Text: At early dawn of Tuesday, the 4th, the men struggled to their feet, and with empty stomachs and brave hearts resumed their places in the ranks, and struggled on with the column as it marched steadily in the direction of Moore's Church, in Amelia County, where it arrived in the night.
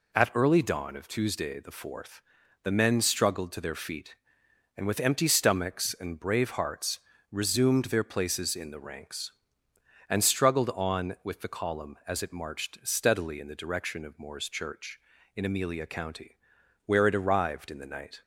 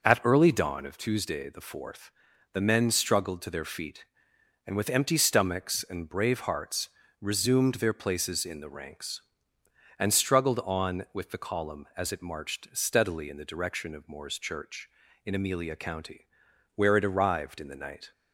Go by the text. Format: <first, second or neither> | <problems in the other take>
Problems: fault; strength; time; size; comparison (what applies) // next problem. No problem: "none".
first | starts louder than the rest; noticeable; until 1.0 s; 5 dB // pauses between "hearts" and "resumed"; slight; at 6.8 s; 0.30 s long; slight in the first